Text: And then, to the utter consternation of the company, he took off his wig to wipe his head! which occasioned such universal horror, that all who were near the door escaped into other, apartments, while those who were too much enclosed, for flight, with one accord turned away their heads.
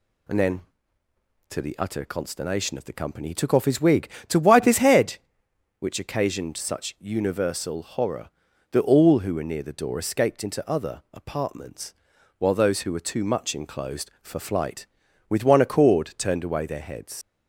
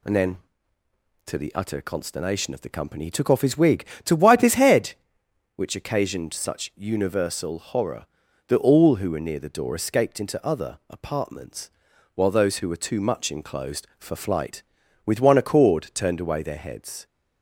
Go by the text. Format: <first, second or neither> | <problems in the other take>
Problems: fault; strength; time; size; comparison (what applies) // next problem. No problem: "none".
second | leaves "heads" unfinished; at 17.2 s; 70 ms